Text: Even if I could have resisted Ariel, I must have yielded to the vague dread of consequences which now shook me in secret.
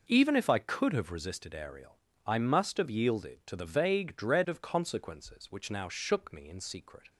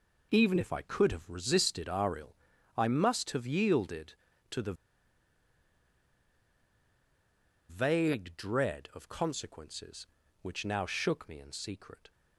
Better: first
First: none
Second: pauses between "the" and "vague"; strong; at 4.7 s; 2.9 s long

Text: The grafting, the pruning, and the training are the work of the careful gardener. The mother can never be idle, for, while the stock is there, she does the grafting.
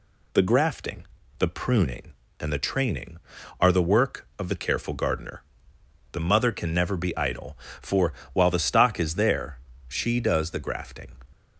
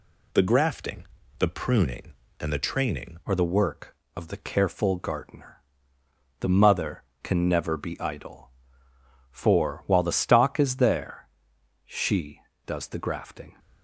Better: first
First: none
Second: changes voice at "are"; from 3.2 s on; 10.3 s long

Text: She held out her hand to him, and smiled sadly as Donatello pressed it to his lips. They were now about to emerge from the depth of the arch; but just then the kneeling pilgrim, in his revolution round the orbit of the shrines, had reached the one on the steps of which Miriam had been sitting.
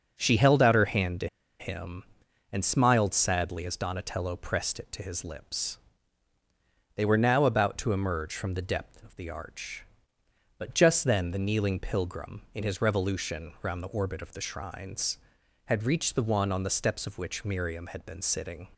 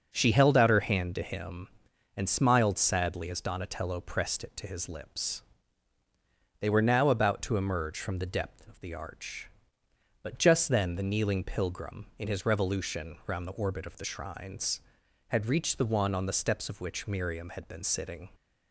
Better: second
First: starts louder than the rest; until 1.1 s; 6 dB // pauses between "to" and "him"; slight; at 1.2 s; 0.32 s long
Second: starts louder than the rest; until 1.1 s; 6 dB

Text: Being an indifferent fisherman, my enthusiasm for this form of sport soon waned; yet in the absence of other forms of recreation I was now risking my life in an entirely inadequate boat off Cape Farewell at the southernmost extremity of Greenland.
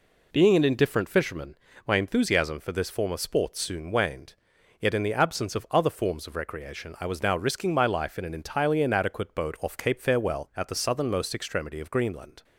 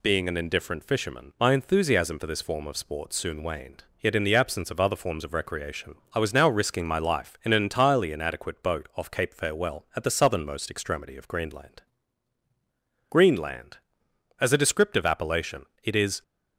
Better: first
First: none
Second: pauses between "recreation" and "I"; slight; at 5.9 s; 0.20 s long // goes on to say "Greenland As a descriptive appellation it is"; strong; from 13.1 s on; 3.1 s long

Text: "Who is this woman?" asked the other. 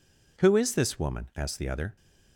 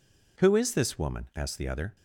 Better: neither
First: none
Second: none

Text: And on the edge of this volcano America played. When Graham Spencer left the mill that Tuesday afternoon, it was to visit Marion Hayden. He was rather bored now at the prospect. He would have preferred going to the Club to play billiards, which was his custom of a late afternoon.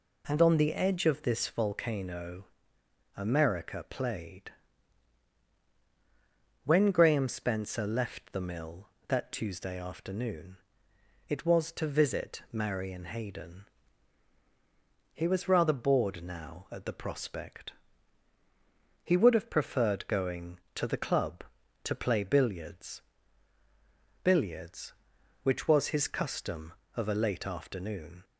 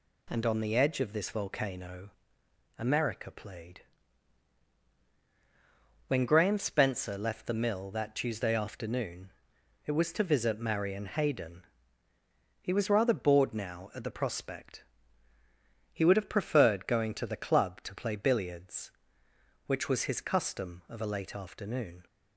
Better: second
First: pauses between "volcano" and "America"; noticeable; at 2.4 s; 0.70 s long // says "billiards" twice; at 24.2 s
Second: pauses between "volcano" and "America"; noticeable; at 2.1 s; 0.66 s long

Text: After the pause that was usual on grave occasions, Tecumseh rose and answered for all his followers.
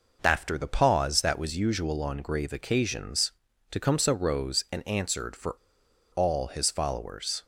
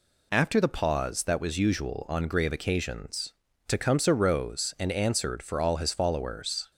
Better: second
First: pauses between "for" and "all"; noticeable; at 5.5 s; 0.60 s long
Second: none

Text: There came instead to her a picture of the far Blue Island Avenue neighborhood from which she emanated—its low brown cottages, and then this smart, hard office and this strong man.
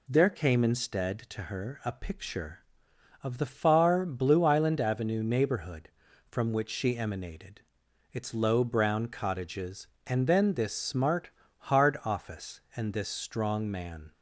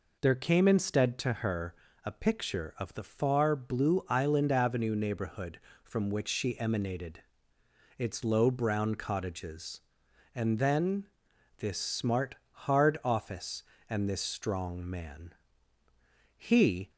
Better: first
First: none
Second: pauses between "her" and "a"; slight; at 1.7 s; 0.30 s long // pauses between "then" and "this"; noticeable; at 11.0 s; 0.52 s long // goes on to say "He"; from 16.3 s on; 0.54 s long

